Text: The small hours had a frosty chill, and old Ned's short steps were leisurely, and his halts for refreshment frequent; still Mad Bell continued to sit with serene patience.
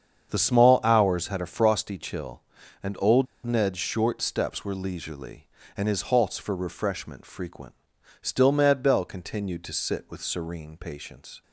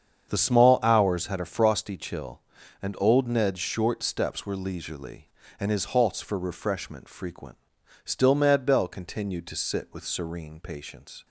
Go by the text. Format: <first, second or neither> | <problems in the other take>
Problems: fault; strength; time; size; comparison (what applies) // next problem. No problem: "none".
second | starts louder than the rest; strong; until 1.3 s; 7.5 dB; strong in the second // pauses between "old" and "Ned's"; slight; at 3.2 s; 0.20 s long